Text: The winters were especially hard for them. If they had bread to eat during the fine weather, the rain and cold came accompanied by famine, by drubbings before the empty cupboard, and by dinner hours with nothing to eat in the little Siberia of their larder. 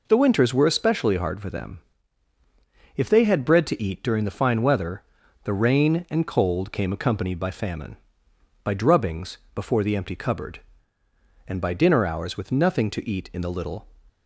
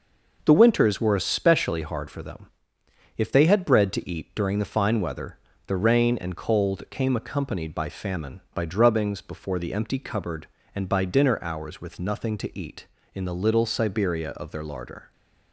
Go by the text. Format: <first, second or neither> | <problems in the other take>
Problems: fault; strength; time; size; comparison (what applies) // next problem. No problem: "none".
second | pauses between "drubbings" and "before"; slight; at 9.3 s; 0.16 s long // stops before "Siberia of their larder"; at 14.0 s